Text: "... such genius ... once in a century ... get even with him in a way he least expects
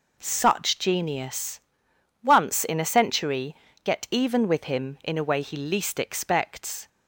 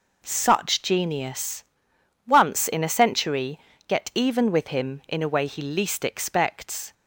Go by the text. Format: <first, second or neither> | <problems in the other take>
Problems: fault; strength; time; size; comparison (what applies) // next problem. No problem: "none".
neither | none